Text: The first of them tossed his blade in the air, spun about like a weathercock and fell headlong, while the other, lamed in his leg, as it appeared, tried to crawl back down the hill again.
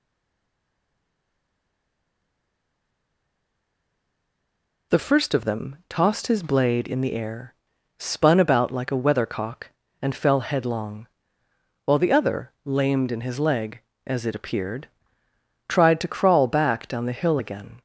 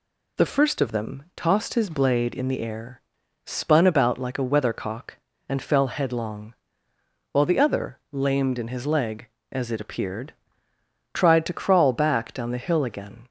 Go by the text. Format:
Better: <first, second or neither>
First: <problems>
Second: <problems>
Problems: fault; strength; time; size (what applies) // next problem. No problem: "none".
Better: second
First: stays silent before the first word; strong; until 4.9 s; 4.9 s long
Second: none